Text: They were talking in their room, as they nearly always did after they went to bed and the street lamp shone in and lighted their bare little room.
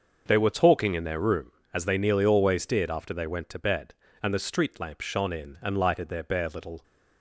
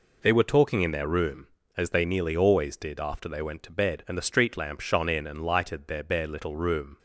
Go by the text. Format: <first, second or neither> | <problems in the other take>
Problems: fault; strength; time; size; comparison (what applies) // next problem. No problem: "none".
second | starts louder than the rest; until 1.2 s; 6.5 dB // stops before "room"; at 6.8 s